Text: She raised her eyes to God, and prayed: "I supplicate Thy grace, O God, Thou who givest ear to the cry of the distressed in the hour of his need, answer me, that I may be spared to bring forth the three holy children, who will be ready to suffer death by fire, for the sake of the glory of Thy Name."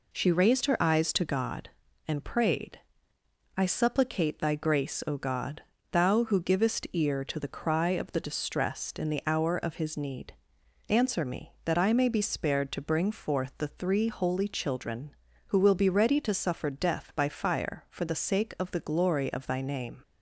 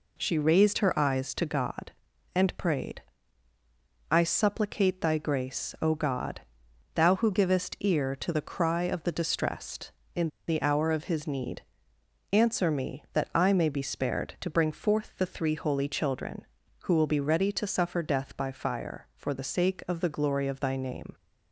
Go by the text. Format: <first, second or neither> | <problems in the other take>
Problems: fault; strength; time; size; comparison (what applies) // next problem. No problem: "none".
first | pauses between "in" and "the"; slight; at 10.2 s; 0.20 s long